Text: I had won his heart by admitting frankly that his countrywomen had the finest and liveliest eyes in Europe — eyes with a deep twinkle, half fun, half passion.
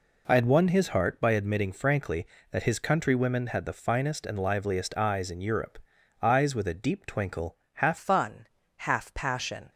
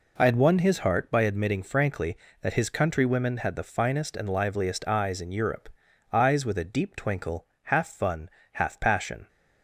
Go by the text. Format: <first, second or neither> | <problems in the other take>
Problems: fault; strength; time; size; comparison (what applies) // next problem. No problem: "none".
second | changes voice at "fun"; from 7.9 s on; 1.8 s long